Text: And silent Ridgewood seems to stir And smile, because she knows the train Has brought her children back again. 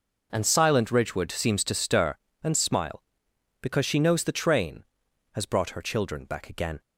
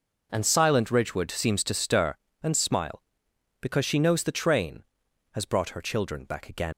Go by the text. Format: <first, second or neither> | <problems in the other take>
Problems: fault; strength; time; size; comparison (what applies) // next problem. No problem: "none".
first | leaves "again" unfinished; at 6.7 s; 80 ms